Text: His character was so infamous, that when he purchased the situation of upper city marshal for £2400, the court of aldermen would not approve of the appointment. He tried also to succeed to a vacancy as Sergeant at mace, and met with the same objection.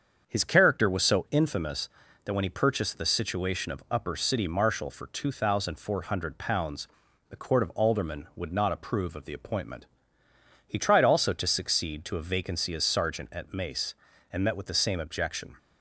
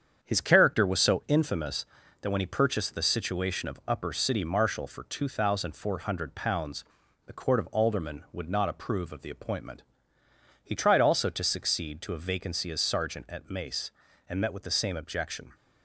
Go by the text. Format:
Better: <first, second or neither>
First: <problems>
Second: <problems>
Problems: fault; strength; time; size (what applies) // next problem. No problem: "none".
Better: first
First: starts louder than the rest; until 1.2 s; 7 dB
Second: gets quieter; noticeable; throughout; 5 dB // starts louder than the rest; strong; until 1.2 s; 7.5 dB